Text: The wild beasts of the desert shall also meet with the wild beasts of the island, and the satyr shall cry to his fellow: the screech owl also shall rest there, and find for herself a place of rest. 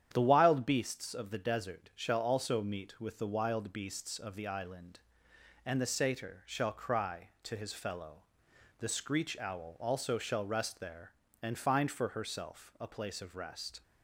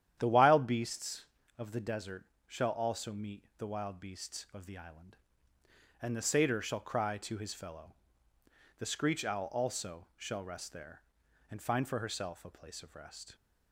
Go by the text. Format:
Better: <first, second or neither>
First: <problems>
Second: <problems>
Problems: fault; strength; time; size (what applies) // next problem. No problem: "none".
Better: first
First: starts louder than the rest; strong; until 1.1 s; 9.5 dB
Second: starts louder than the rest; strong; until 1.1 s; 10.5 dB // pauses between "desert" and "shall"; slight; at 2.2 s; 0.24 s long // skips "with"; at 3.5 s